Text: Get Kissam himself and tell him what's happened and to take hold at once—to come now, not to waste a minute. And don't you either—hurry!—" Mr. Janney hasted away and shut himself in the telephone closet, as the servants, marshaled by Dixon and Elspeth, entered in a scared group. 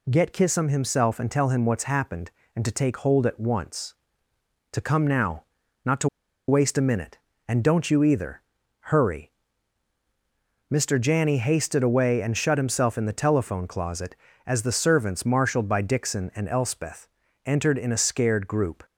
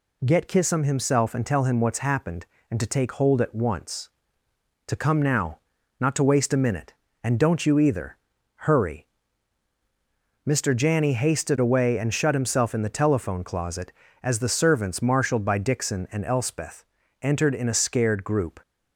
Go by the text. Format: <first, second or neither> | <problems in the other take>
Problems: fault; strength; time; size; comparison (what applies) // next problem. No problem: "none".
second | pauses between "to" and "waste"; at 6.0 s; 0.40 s long